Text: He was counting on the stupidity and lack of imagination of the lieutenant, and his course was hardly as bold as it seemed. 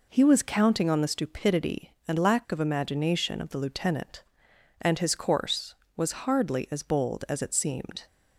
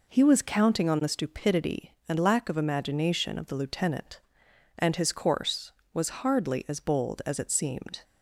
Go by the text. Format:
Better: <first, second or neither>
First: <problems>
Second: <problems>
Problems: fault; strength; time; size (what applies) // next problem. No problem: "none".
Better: neither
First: none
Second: none